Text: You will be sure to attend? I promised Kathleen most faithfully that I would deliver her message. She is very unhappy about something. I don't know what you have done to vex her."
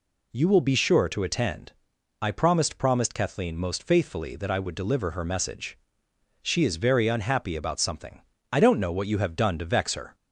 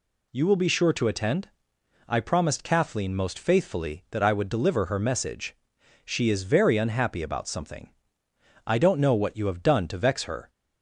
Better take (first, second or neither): second